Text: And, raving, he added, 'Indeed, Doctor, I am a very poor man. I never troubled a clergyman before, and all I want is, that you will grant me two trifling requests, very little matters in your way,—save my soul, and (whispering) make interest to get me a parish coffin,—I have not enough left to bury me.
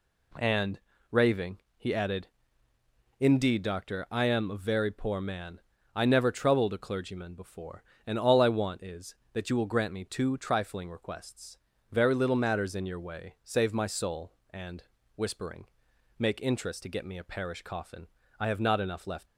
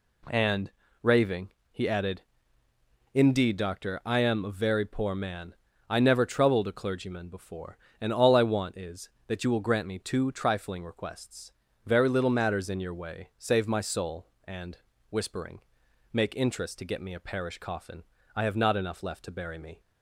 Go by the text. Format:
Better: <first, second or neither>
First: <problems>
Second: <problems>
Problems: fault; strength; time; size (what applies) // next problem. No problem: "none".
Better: second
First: stops before "to bury me"; at 19.2 s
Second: none